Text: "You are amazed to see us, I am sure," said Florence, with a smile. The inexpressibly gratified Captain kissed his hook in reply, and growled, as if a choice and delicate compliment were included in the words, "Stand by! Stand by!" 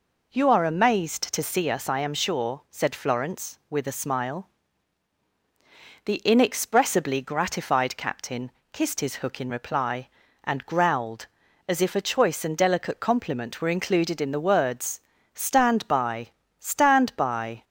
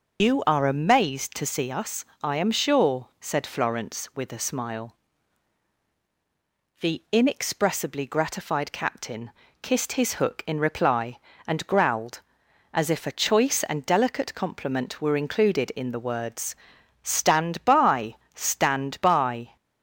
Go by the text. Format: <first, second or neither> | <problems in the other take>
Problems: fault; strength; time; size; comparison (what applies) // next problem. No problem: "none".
first | loses the start of "You"; at 0.1 s; 100 ms // starts louder than the rest; noticeable; until 1.2 s; 6 dB // pauses between "Captain" and "kissed"; slight; at 9.3 s; 0.28 s long; slight in the first